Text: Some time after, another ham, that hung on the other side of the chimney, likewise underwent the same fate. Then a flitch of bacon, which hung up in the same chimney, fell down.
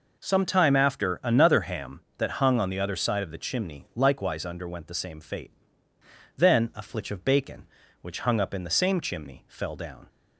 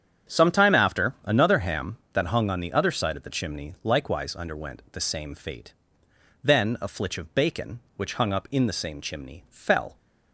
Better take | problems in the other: first | starts louder than the rest; strong; until 1.3 s; 8.5 dB // stops before "down"; at 9.9 s

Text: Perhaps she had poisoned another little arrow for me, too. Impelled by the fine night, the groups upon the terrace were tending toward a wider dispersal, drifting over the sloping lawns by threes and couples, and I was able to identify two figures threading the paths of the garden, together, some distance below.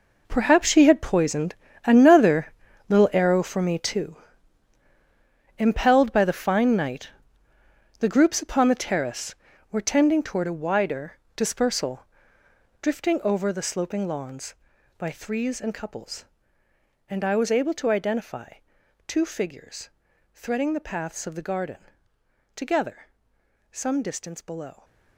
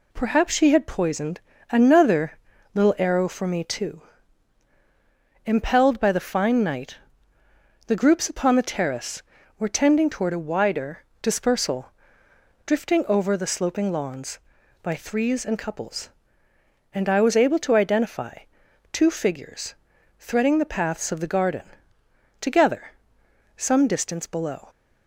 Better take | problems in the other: second | gets quieter; strong; throughout; 13 dB // pauses between "poisoned" and "another"; slight; at 1.5 s; 0.30 s long; slight in the second // pauses between "another" and "little"; at 2.5 s; 0.38 s long; also in the second // pauses between "wider" and "dispersal"; slight; at 11.1 s; 0.18 s long; slight in the second // pauses between "identify" and "two"; noticeable; at 18.5 s; 0.52 s long; noticeable in the second // pauses between "figures" and "threading"; noticeable; at 19.8 s; 0.46 s long; noticeable in the second

